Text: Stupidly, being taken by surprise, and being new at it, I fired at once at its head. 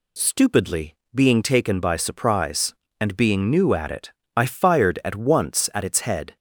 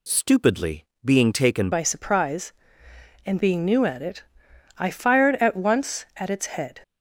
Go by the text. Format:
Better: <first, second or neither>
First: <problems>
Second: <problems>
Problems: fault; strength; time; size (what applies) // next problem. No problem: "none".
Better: first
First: none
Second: changes voice at "by"; from 1.7 s on; 5.1 s long